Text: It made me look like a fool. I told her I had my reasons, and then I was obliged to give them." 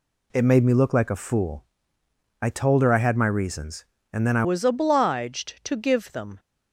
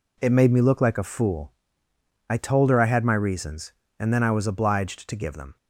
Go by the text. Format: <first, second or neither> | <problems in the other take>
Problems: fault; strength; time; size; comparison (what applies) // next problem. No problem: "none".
second | changes voice at "was"; from 4.4 s on; 1.9 s long